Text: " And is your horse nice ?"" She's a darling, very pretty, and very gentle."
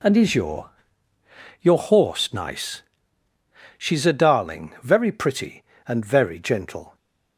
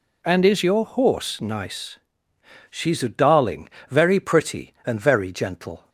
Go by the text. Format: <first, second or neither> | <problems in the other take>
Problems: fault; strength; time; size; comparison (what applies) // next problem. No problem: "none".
second | says "your" twice; at 1.6 s